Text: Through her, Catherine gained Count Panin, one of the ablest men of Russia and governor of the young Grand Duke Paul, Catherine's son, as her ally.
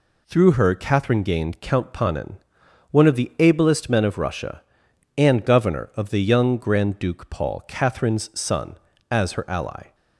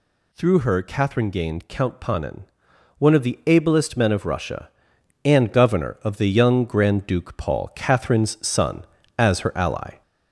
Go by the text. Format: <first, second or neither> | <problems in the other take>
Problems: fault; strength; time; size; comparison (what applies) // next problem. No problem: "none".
first | gets louder; slight; throughout; 3 dB